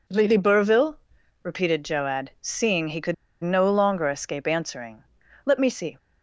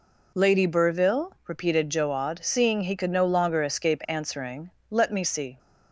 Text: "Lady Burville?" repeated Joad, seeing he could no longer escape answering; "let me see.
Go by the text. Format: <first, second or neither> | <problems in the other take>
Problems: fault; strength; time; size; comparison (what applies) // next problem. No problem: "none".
second | pauses between "could" and "no"; slight; at 3.1 s; 0.29 s long